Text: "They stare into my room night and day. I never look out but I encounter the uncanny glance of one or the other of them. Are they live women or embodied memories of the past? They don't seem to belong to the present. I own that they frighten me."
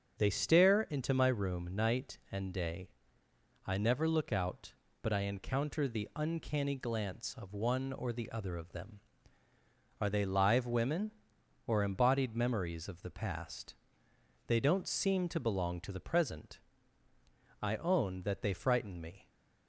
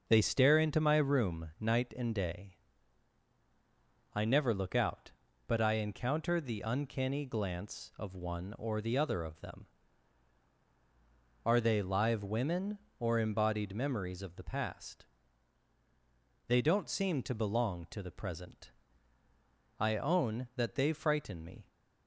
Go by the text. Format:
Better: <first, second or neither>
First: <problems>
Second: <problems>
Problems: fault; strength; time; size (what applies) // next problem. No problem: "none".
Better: neither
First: starts louder than the rest; strong; until 1.1 s; 7 dB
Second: starts louder than the rest; noticeable; until 1.0 s; 6 dB